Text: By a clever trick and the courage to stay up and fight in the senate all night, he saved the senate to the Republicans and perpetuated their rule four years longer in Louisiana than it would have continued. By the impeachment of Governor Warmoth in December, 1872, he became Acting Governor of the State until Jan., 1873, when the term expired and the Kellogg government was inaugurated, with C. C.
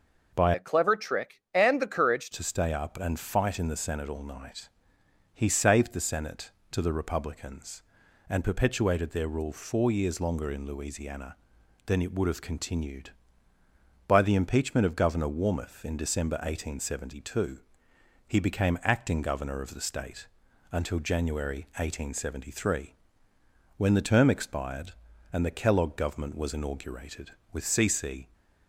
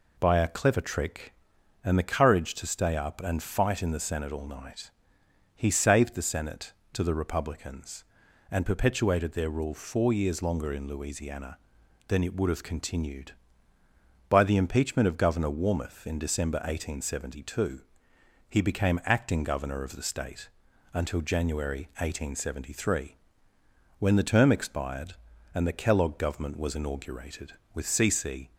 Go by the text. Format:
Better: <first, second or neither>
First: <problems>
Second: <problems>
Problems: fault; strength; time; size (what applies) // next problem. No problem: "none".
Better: second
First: changes voice from "a" to "courage"; from 0.5 to 2.3 s; 1.8 s long // pauses between "State" and "until"; noticeable; at 20.2 s; 0.46 s long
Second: pauses between "State" and "until"; noticeable; at 20.4 s; 0.46 s long